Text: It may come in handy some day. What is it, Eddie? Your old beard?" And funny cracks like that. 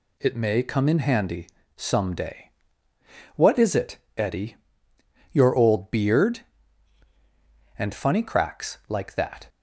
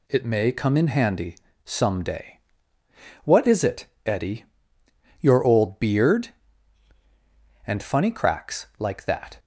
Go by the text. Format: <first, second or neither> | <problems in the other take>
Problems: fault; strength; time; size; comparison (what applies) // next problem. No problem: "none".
neither | pauses between "handy" and "some"; slight; the same in both